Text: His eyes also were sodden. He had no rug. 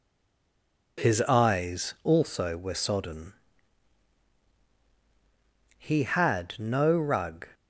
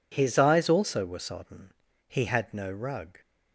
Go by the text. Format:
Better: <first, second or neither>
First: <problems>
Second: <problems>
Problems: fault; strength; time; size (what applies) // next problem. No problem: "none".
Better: second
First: stays silent before the first word; slight; until 0.9 s; 0.9 s long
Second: none